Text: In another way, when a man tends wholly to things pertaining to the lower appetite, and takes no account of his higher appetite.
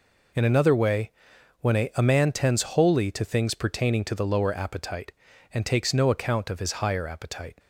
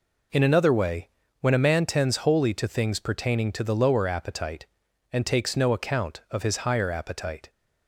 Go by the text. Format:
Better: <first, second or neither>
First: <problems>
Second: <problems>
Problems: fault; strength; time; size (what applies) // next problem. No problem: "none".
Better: second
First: says "a" twice; at 1.9 s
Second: none